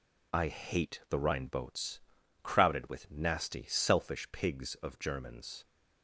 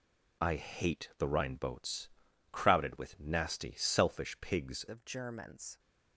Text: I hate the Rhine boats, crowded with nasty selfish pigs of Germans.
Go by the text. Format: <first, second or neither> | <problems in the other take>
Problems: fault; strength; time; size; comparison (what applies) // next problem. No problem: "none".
first | changes voice at "of"; from 4.8 s on; 0.9 s long